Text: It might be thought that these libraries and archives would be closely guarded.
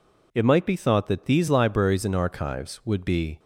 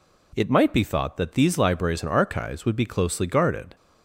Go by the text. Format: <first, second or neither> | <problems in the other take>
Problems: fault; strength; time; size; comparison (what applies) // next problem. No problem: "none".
second | stops before "closely guarded"; at 3.3 s